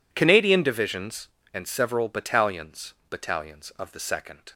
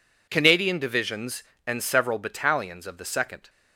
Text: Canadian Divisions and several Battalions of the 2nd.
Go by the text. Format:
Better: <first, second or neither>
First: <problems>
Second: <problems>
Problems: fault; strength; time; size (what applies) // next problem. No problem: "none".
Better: second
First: says "Battalions" twice; at 3.0 s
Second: none